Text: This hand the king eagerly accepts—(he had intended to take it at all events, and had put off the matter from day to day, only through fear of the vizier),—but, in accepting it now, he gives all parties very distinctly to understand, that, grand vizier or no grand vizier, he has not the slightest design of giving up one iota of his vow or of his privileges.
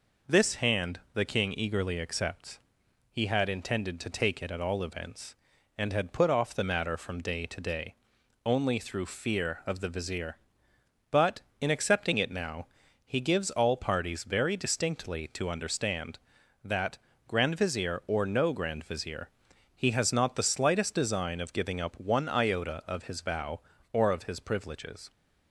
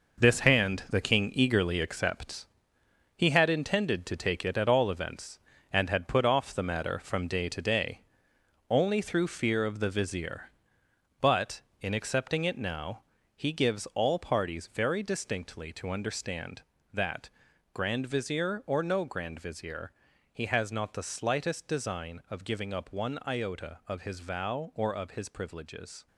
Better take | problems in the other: first | gets quieter; throughout; 3.5 dB

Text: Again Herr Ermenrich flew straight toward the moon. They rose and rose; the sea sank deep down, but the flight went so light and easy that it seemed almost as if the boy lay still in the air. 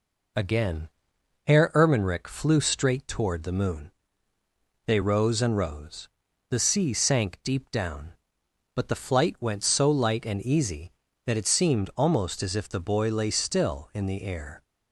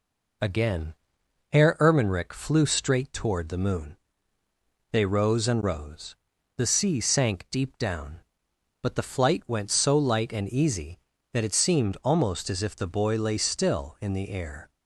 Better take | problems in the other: neither | pauses between "Again" and "Herr"; noticeable; the same in both

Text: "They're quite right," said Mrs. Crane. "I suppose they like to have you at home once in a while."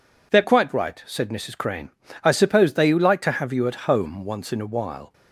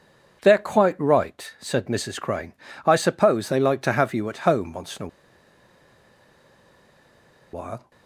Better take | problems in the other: first | pauses between "a" and "while"; strong; at 5.0 s; 2.4 s long

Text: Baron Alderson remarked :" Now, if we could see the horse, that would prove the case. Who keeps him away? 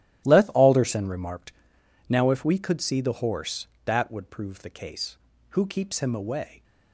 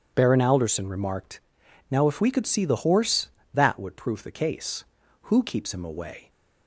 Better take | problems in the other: second | starts louder than the rest; strong; until 1.3 s; 11.5 dB // says "Leth" for "Baron"; at 0.2 s

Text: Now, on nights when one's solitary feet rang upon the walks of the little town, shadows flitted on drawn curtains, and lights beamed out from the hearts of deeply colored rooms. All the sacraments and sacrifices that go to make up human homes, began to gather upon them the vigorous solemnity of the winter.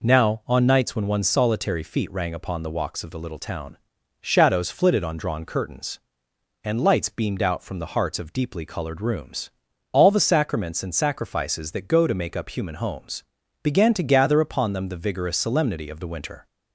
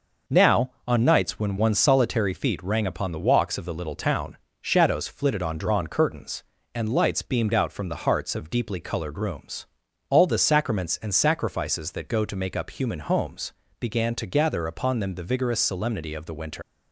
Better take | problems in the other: first | leaves "winter" unfinished; at 16.6 s; 125 ms

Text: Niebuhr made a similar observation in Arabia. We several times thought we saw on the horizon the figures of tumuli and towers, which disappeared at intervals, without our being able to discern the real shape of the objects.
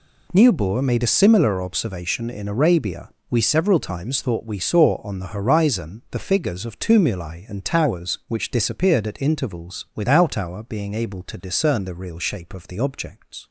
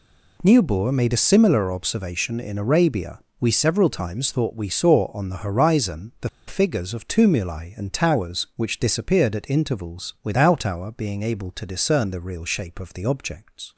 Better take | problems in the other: first | pauses between "the" and "figures"; slight; at 6.2 s; 0.19 s long

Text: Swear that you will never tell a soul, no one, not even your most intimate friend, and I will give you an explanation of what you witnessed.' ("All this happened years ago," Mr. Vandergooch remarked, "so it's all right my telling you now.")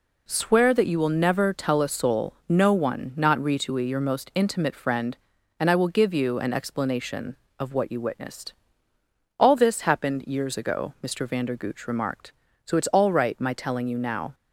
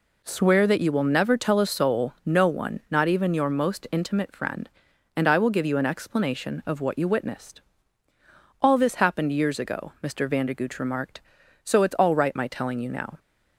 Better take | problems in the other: second | says "ritui" for "even"; at 3.3 s

